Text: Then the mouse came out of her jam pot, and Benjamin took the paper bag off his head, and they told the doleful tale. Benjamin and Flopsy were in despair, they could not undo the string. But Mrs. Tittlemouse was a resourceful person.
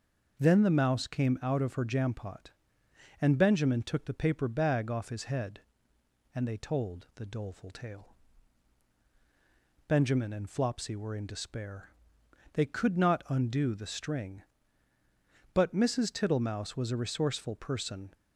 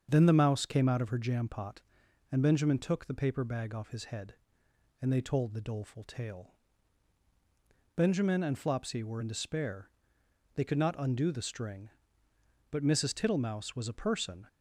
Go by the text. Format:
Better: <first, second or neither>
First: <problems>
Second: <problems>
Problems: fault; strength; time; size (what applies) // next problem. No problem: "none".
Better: first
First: none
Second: starts louder than the rest; strong; until 1.1 s; 7 dB // skips "resourceful"; at 13.9 s